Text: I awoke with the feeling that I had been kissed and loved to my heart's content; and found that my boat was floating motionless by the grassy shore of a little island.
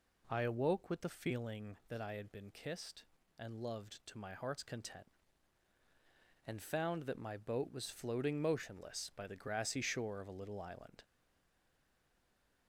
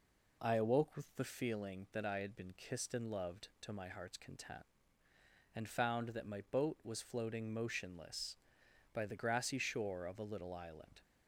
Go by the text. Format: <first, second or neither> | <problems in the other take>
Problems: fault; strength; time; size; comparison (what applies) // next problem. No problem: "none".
second | stays silent after the last word; noticeable; from 11.0 s on; 1.6 s long